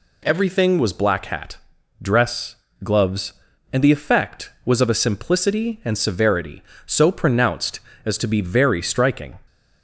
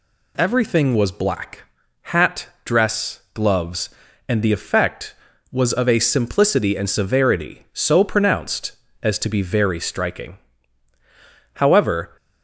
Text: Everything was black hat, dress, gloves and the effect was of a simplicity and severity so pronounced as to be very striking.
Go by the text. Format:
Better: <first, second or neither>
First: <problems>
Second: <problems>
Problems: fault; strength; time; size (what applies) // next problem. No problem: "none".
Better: first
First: none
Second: pauses between "black" and "hat"; at 1.6 s; 0.40 s long // goes on to say "However"; noticeable; from 11.5 s on; 0.62 s long